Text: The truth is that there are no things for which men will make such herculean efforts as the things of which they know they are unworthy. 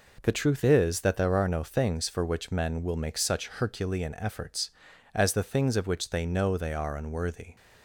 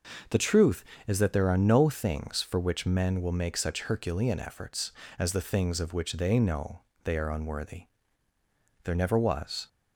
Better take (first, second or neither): first